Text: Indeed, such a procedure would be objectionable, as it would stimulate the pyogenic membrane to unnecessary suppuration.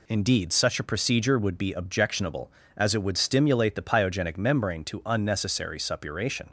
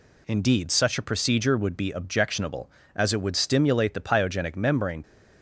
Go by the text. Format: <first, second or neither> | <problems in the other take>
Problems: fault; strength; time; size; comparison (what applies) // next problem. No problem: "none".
first | stops before "to unnecessary suppuration"; at 5.0 s